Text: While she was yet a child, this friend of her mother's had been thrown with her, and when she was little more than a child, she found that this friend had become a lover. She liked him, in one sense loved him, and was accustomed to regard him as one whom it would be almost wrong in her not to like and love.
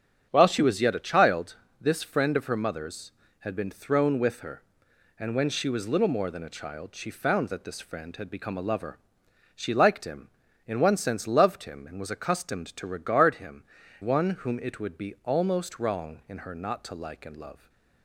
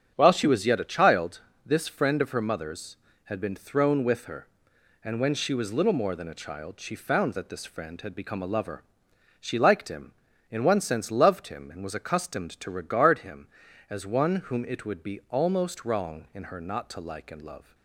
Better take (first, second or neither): second